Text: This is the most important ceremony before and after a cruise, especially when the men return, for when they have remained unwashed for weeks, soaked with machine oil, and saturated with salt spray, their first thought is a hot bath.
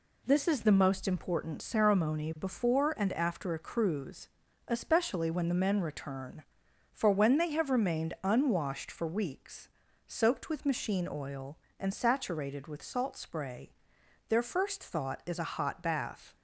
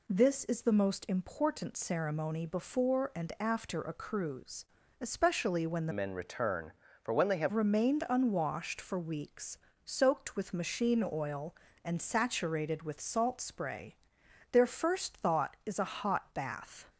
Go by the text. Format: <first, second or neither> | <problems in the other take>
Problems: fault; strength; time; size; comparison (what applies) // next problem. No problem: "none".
first | changes voice from "men" to "have"; from 5.9 to 7.5 s; 1.6 s long